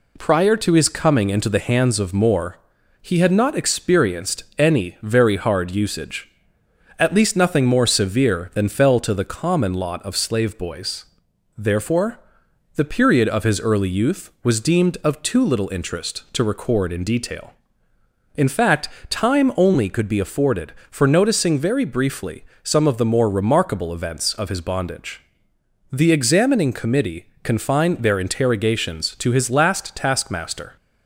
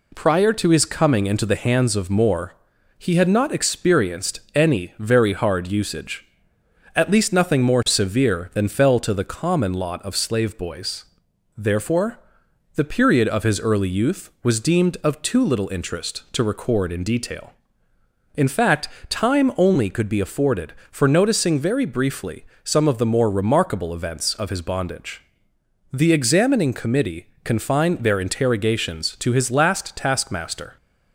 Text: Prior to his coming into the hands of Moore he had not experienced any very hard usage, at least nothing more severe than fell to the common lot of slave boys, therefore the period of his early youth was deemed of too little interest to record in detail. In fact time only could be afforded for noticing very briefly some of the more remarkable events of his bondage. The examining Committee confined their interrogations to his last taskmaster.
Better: neither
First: pauses between "Moore" and "he"; noticeable; at 2.5 s; 0.46 s long // pauses between "experienced" and "any"; slight; at 4.4 s; 0.16 s long // pauses between "therefore" and "the"; noticeable; at 12.1 s; 0.56 s long // pauses between "fact" and "time"; slight; at 18.8 s; 0.22 s long // pauses between "briefly" and "some"; slight; at 22.4 s; 0.18 s long // pauses between "Committee" and "confined"; slight; at 27.2 s; 0.18 s long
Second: pauses between "Moore" and "he"; noticeable; at 2.5 s; 0.46 s long // pauses between "experienced" and "any"; slight; at 4.3 s; 0.16 s long // pauses between "therefore" and "the"; noticeable; at 12.1 s; 0.56 s long // pauses between "fact" and "time"; slight; at 18.8 s; 0.22 s long // pauses between "briefly" and "some"; slight; at 22.4 s; 0.18 s long // pauses between "Committee" and "confined"; slight; at 27.2 s; 0.18 s long

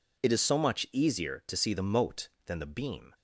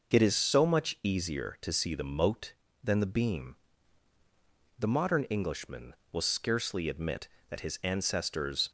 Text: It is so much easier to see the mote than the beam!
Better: first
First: none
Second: goes on to say "The modern Englishman will scarcely admit that his ancestors"; strong; from 4.7 s on; 3.9 s long

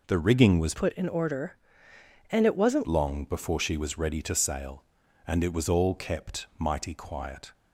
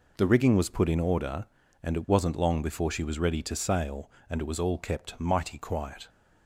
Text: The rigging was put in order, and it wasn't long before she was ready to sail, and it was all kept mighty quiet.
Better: second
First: changes voice from "put" to "wasn't"; from 0.7 to 2.8 s; 2.1 s long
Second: none

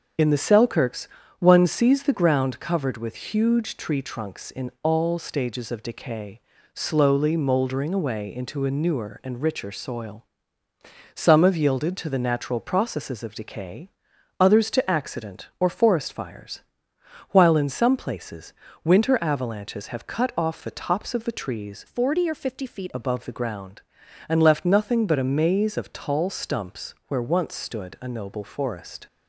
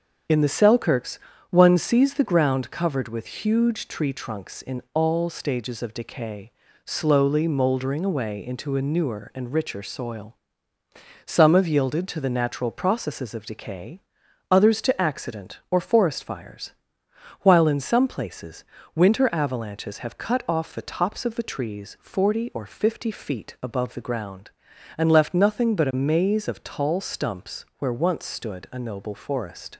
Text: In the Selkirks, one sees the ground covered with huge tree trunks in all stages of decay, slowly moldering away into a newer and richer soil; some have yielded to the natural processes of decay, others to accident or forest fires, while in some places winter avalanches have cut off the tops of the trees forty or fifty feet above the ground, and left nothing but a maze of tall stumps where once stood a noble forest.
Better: second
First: starts louder than the rest; until 1.4 s; 6.5 dB // pauses between "places" and "winter"; slight; at 18.5 s; 0.32 s long // changes voice from "forty" to "feet"; from 21.8 to 22.9 s; 1.1 s long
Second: starts louder than the rest; until 1.6 s; 6.5 dB // pauses between "places" and "winter"; slight; at 18.6 s; 0.32 s long

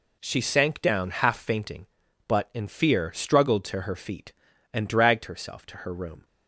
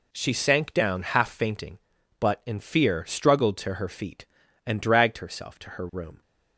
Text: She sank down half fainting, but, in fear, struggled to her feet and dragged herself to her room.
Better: neither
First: none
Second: none

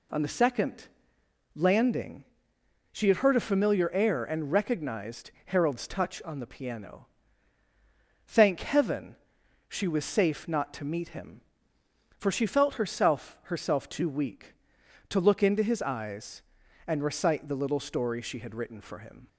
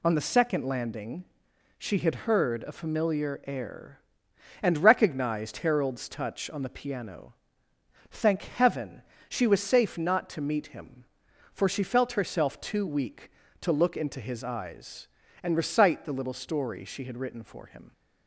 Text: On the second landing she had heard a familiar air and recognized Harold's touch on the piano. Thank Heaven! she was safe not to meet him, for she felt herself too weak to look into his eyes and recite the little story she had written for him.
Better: second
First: pauses between "second" and "landing"; noticeable; at 0.8 s; 0.66 s long // pauses between "landing" and "she"; noticeable; at 2.2 s; 0.68 s long // pauses between "recognized" and "Harold's"; slight; at 5.3 s; 0.16 s long // says "herself" twice; at 13.4 s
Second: pauses between "landing" and "she"; noticeable; at 1.2 s; 0.52 s long

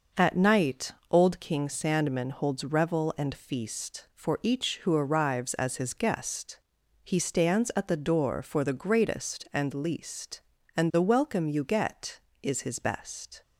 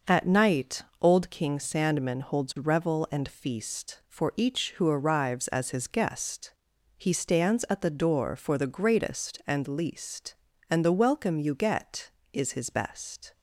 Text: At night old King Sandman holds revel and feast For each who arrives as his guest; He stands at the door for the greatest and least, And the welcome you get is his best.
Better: neither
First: pauses between "night" and "old"; slight; at 0.9 s; 0.20 s long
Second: pauses between "night" and "old"; slight; at 0.8 s; 0.20 s long

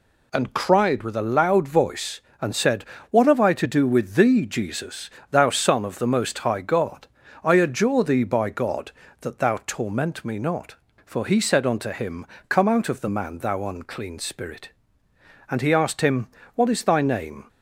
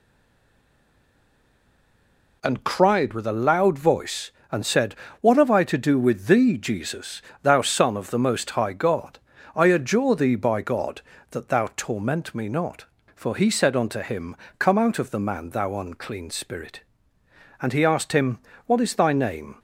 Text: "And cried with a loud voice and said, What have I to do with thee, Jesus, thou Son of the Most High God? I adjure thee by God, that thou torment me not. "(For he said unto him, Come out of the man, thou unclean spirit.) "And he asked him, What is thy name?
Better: first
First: none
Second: stays silent before the first word; until 2.4 s; 2.4 s long

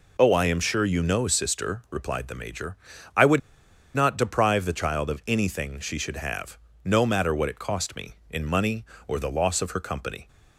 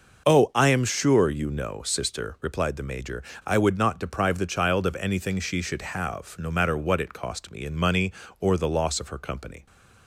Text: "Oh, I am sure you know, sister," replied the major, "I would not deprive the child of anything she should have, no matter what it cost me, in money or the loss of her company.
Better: second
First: pauses between "would" and "not"; noticeable; at 3.4 s; 0.55 s long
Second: none

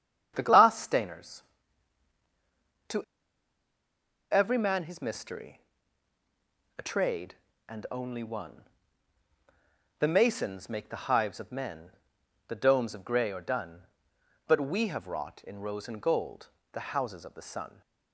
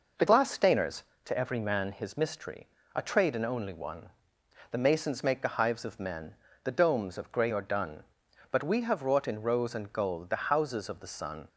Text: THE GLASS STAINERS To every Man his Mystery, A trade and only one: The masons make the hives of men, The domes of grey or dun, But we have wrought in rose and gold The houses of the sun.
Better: second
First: starts louder than the rest; strong; until 1.3 s; 8.5 dB // pauses between "To" and "every"; strong; at 3.0 s; 1.2 s long // pauses between "gold" and "The"; slight; at 16.4 s; 0.26 s long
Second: none

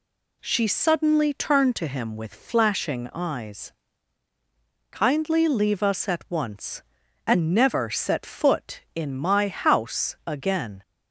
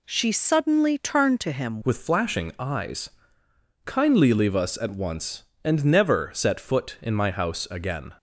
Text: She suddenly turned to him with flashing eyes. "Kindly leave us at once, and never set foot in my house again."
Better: first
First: none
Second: changes voice at "with"; from 1.8 s on; 6.3 s long

